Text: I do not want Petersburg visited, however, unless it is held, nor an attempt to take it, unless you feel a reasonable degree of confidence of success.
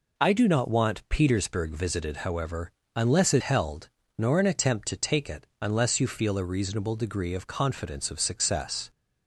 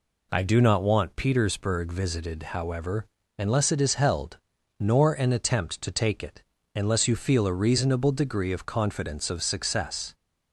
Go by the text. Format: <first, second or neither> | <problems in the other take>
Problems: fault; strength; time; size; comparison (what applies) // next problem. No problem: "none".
second | skips "is"; at 3.4 s